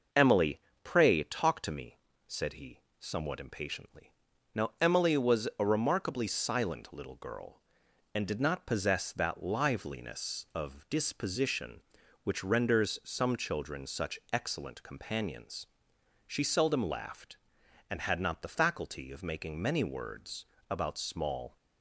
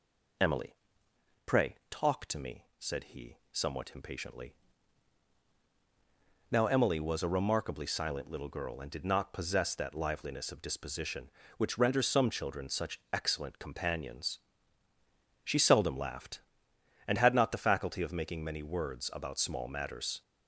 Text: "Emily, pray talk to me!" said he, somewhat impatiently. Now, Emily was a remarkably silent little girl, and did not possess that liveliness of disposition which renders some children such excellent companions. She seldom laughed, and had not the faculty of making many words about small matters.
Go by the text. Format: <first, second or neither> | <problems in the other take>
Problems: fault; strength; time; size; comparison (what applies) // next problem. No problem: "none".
second | pauses between "words" and "about"; slight; at 20.4 s; 0.24 s long // stops before "matters"; at 21.5 s